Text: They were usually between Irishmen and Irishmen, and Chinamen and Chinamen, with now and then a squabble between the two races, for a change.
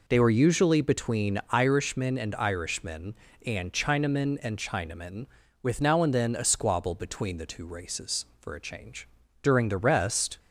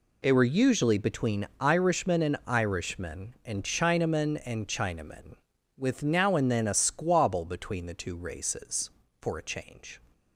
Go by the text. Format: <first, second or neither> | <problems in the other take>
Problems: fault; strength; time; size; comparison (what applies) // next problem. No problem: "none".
second | goes on to say "During the rest"; noticeable; from 9.4 s on; 0.96 s long